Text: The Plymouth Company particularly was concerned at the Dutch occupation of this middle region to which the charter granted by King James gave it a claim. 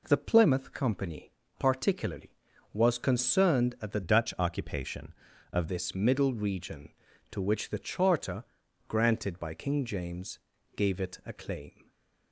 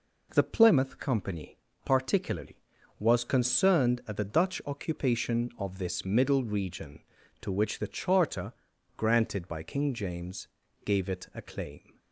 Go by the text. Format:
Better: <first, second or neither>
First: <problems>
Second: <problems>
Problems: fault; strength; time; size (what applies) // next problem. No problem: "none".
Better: second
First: pauses between "Company" and "particularly"; slight; at 1.3 s; 0.26 s long // changes voice from "Dutch" to "of"; from 4.0 to 5.6 s; 1.6 s long // pauses between "charter" and "granted"; noticeable; at 8.4 s; 0.46 s long // pauses between "James" and "gave"; slight; at 10.3 s; 0.34 s long // stays silent after the last word; slight; from 11.8 s on; 0.5 s long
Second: pauses between "Company" and "particularly"; slight; at 1.5 s; 0.26 s long // pauses between "charter" and "granted"; noticeable; at 8.5 s; 0.46 s long // pauses between "James" and "gave"; slight; at 10.4 s; 0.34 s long